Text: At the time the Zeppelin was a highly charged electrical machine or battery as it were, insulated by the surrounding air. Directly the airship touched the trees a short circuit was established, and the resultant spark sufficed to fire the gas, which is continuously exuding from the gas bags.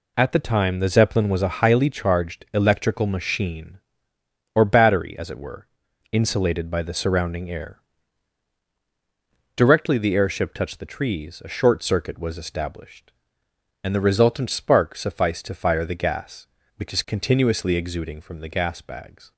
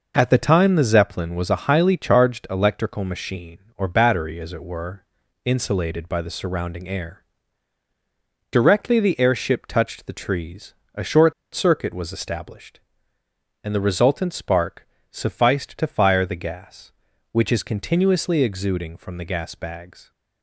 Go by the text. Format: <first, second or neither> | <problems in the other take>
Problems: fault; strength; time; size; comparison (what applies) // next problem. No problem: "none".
first | pauses between "trees" and "a"; slight; at 10.7 s; 0.20 s long // pauses between "short" and "circuit"; slight; at 11.3 s; 0.21 s long // pauses between "spark" and "sufficed"; slight; at 14.8 s; 0.24 s long